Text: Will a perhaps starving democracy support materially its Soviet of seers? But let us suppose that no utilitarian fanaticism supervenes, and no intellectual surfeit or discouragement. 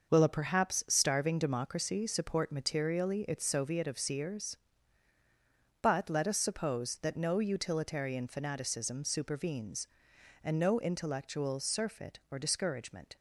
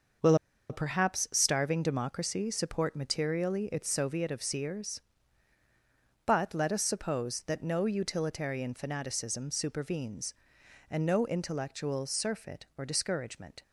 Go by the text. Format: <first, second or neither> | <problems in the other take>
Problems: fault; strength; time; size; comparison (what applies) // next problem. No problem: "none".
first | starts louder than the rest; until 1.6 s; 6 dB; also in the first // pauses between "Will" and "a"; slight; at 0.3 s; 0.33 s long